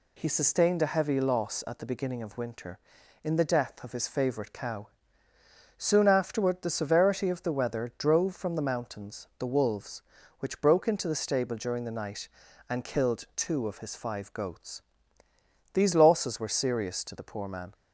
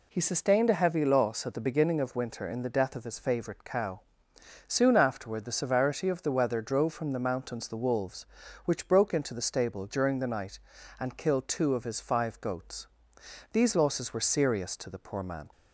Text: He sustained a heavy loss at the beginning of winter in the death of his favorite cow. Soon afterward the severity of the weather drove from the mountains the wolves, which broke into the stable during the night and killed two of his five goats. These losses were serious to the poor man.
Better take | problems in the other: neither | none

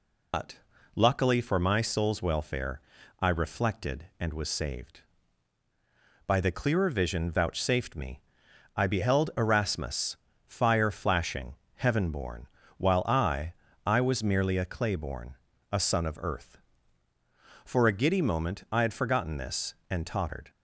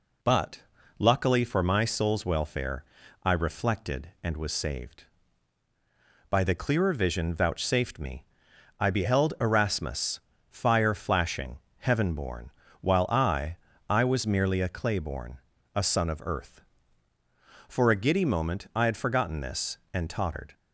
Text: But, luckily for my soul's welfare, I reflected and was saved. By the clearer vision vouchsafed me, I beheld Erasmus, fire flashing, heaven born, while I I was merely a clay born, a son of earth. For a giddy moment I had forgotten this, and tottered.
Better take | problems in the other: second | loses the start of "But"; at 0.3 s; 140 ms // pauses between "I" and "I"; slight; at 13.5 s; 0.32 s long; slight in the second

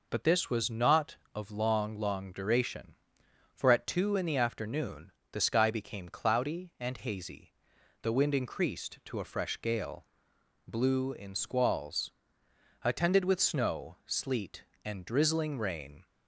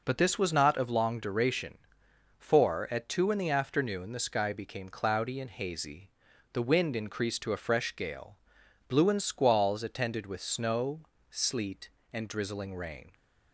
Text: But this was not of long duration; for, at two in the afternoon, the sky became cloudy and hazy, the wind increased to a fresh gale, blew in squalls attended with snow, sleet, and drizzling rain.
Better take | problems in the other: second | says "long" twice; at 1.9 s // pauses between "squalls" and "attended"; noticeable; at 12.1 s; 0.70 s long

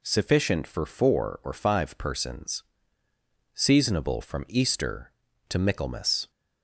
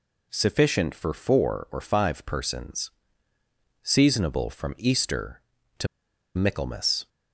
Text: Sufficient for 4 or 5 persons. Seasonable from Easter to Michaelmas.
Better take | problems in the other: first | pauses between "to" and "Michaelmas"; noticeable; at 5.8 s; 0.49 s long

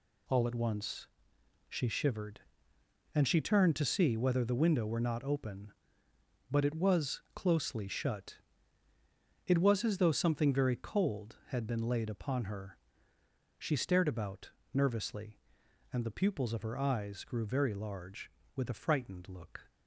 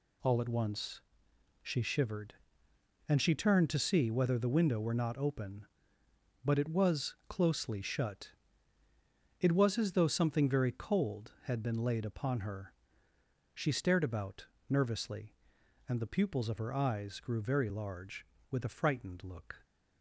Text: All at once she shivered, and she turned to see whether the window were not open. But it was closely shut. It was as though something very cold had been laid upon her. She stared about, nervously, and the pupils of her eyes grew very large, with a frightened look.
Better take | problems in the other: neither | pauses between "once" and "she"; noticeable; the same in both

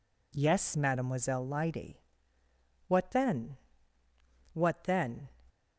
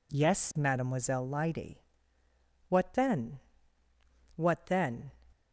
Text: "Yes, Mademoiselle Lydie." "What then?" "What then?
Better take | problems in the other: neither | none

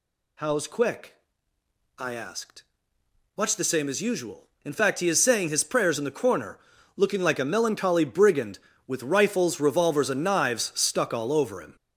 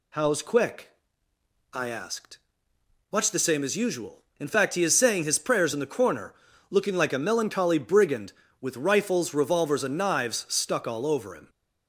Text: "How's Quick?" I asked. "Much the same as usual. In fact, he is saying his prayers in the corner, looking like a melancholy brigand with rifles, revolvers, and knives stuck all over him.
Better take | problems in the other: second | gets louder; throughout; 6.5 dB

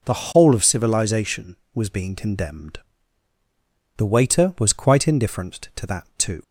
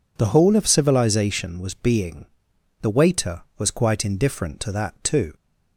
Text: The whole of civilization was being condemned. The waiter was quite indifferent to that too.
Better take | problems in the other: first | skips "condemned"; at 2.5 s

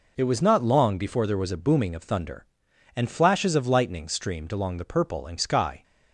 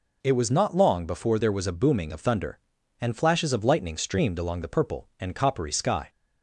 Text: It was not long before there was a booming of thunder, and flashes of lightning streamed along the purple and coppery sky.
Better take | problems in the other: second | skips "coppery"; at 5.3 s

